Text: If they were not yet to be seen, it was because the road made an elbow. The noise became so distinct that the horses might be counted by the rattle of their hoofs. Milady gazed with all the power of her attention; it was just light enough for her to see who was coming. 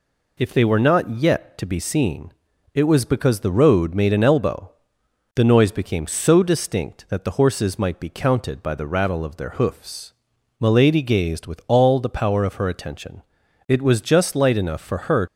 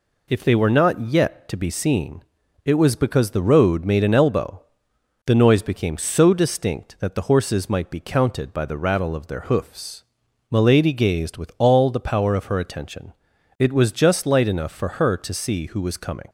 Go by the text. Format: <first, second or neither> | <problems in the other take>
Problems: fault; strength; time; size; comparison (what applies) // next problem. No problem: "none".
second | stops before "to see who was coming"; at 15.2 s